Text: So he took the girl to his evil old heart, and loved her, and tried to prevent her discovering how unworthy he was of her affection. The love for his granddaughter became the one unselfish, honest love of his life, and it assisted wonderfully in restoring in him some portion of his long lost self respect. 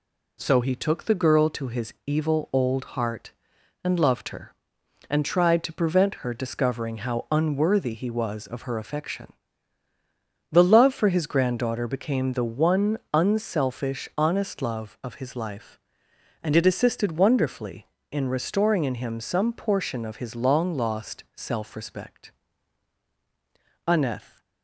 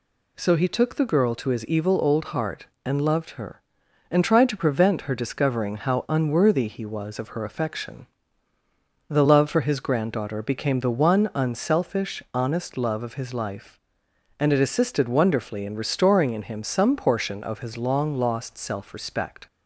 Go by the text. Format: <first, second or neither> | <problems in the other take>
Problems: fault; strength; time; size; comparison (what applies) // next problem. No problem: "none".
second | goes on to say "Aneth"; from 23.8 s on; 0.52 s long